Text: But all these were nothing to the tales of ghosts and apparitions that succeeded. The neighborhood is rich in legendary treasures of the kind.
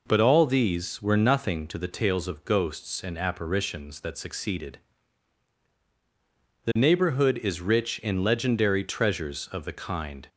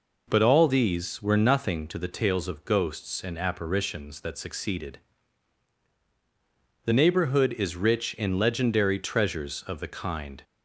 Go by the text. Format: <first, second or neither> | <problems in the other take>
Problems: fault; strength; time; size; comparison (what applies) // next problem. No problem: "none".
neither | none